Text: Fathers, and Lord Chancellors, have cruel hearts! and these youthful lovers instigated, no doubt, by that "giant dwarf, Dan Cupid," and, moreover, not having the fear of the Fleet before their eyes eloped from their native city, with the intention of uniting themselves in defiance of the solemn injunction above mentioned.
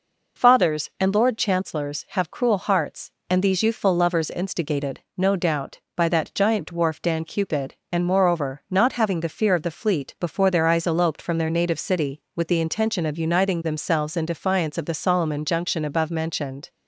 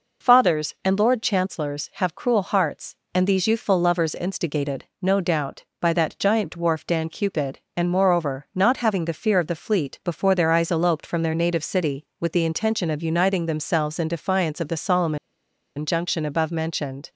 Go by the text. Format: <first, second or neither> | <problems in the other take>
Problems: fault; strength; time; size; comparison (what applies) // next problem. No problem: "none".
first | pauses between "solemn" and "injunction"; noticeable; at 15.1 s; 0.60 s long